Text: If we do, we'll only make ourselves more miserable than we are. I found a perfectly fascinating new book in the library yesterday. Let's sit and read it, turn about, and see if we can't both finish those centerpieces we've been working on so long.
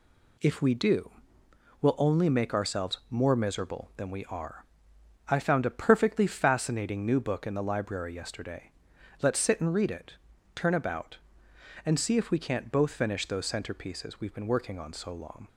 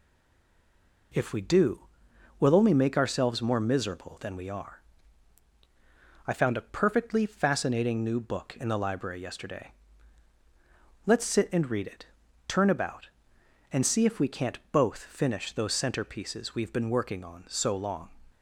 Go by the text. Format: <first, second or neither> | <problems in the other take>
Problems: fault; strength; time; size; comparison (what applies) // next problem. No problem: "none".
first | stays silent before the first word; until 1.1 s; 1.1 s long